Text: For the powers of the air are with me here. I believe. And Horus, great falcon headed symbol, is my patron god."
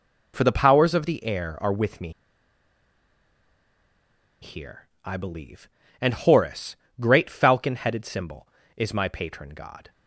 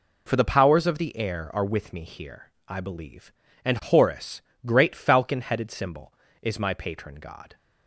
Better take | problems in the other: second | pauses between "me" and "here"; strong; at 2.1 s; 2.3 s long

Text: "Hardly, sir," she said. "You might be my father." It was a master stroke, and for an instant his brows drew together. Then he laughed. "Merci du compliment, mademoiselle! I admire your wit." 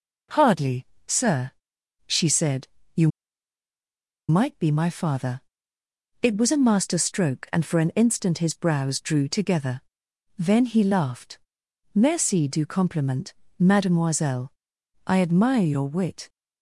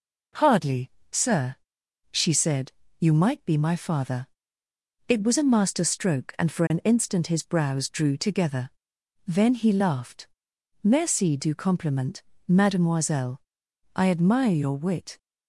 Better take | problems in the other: second | pauses between "You" and "might"; at 3.0 s; 1.2 s long

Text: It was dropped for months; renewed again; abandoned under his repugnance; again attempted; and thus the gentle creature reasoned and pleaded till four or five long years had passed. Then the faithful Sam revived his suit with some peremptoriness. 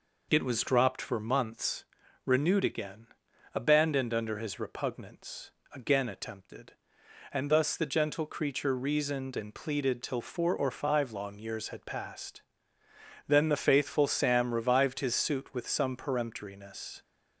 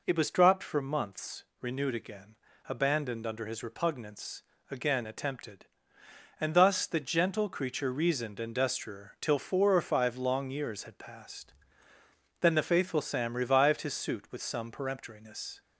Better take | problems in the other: first | says "destrier" for "pleaded"; at 8.5 s

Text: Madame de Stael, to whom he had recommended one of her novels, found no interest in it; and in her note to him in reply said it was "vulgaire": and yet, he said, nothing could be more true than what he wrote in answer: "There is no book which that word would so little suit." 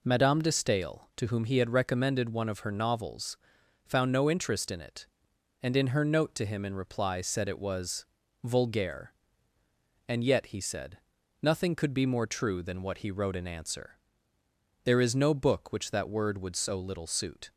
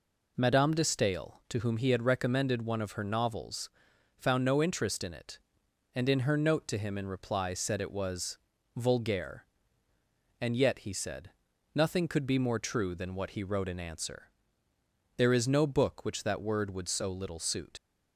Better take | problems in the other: first | pauses between "was" and "vulgaire"; at 8.3 s; 0.38 s long; also in the first // leaves "suit" unfinished; at 17.7 s; 75 ms

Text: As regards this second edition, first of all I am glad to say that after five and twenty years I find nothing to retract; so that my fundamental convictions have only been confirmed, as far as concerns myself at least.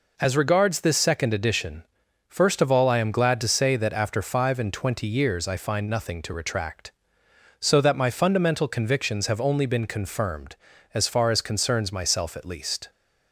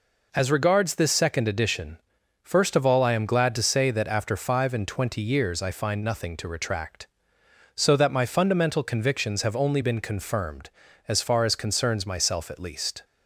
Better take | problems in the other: neither | none

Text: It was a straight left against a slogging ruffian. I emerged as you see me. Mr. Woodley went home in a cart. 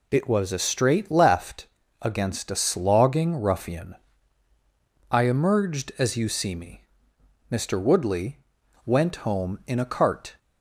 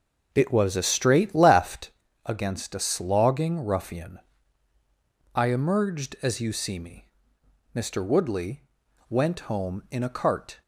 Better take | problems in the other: first | starts louder than the rest; noticeable; until 2.1 s; 5.5 dB // pauses between "left" and "against"; slight; at 1.8 s; 0.34 s long; slight in the first // pauses between "Woodley" and "went"; noticeable; at 8.6 s; 0.48 s long; noticeable in the first

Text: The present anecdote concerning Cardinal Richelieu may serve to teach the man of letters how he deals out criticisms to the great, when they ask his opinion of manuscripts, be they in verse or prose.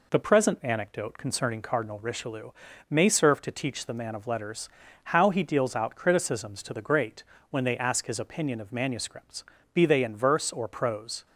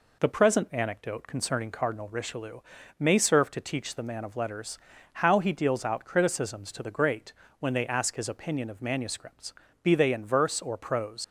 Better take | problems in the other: first | pauses between "Richelieu" and "may"; at 2.5 s; 0.40 s long; also in the first // pauses between "letters" and "how"; at 4.7 s; 0.38 s long; also in the first // leaves "prose" unfinished; at 11.2 s; 100 ms

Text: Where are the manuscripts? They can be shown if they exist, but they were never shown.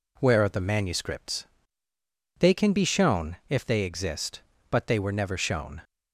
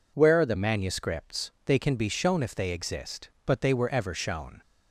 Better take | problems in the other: first | says "ever" for "never"; at 3.8 s

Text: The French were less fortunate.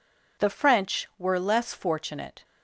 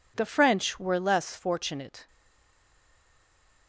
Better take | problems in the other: first | stays silent after the last word; noticeable; from 2.0 s on; 1.6 s long

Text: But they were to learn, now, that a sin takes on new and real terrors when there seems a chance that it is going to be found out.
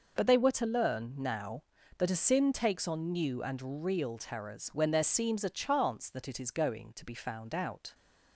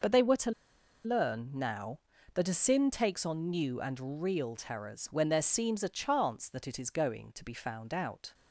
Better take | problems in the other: first | pauses between "to" and "learn"; noticeable; at 0.5 s; 0.54 s long

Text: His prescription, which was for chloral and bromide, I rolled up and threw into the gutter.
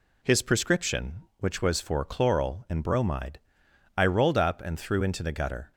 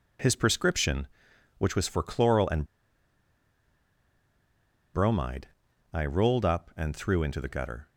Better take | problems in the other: first | pauses between "and" and "bromide"; strong; at 2.6 s; 2.2 s long

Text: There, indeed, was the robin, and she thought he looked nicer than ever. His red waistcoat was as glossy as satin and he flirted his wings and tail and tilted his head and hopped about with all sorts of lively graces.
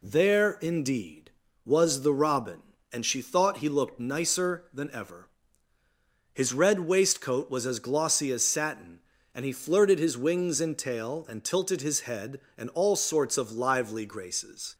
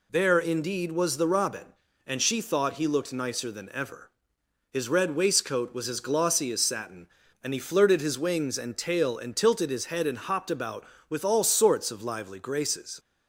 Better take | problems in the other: second | skips "hopped about with"; at 12.7 s

